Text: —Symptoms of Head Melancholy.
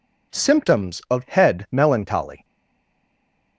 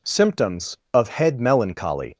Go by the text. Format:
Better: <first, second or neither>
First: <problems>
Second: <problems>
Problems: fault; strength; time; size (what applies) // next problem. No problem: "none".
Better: second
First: stays silent after the last word; from 2.4 s on; 1.1 s long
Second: none